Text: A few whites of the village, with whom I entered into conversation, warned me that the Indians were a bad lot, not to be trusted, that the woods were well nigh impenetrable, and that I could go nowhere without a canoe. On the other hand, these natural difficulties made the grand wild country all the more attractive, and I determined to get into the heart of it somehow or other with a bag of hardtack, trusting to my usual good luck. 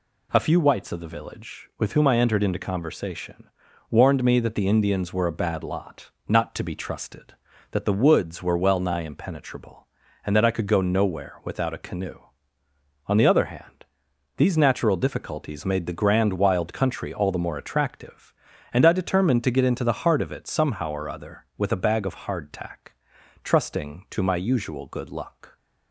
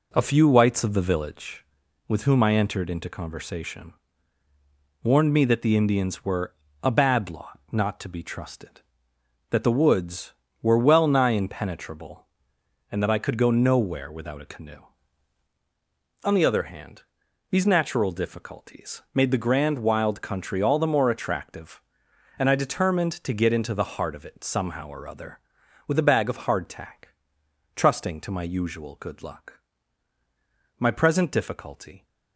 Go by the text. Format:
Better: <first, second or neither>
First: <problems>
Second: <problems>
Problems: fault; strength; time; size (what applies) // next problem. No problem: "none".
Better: first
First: none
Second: pauses between "were" and "a"; slight; at 6.5 s; 0.30 s long // goes on to say "My present difficulty"; noticeable; from 30.7 s on; 1.2 s long